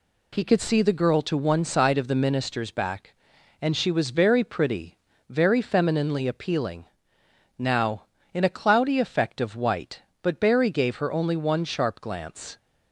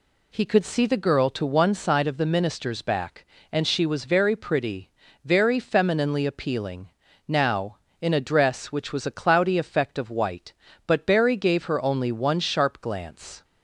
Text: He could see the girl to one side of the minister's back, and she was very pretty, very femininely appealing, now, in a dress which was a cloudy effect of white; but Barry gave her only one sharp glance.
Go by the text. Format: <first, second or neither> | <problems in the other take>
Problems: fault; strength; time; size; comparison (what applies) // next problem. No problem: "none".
second | skips "dress which was a"; at 8.4 s